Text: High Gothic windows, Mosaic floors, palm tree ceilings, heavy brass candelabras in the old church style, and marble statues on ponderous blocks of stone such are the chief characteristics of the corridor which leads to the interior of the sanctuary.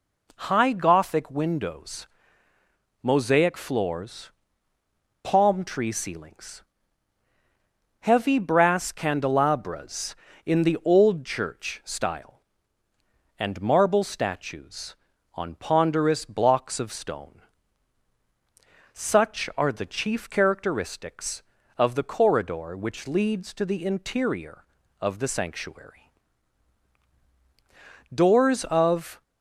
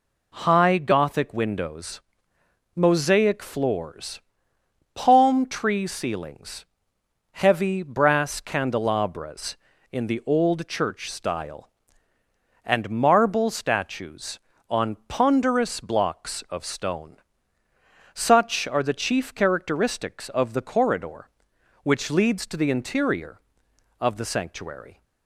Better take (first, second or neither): second